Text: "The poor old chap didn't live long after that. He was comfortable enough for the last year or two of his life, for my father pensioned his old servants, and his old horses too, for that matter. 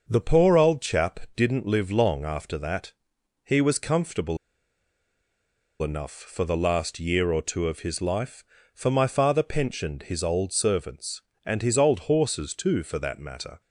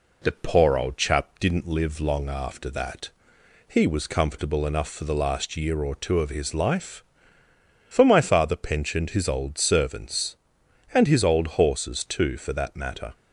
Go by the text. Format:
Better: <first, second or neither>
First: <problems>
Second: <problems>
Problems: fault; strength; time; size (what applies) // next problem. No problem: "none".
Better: second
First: starts louder than the rest; until 1.1 s; 6.5 dB // pauses between "chap" and "didn't"; slight; at 1.1 s; 0.16 s long // pauses between "comfortable" and "enough"; strong; at 4.3 s; 1.4 s long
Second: none